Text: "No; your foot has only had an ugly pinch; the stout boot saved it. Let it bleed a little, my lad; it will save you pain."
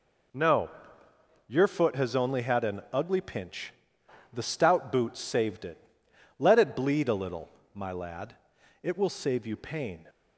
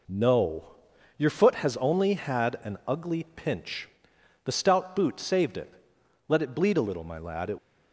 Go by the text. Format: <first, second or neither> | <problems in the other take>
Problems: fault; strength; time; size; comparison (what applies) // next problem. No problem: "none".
first | stops before "will save you pain"; at 7.5 s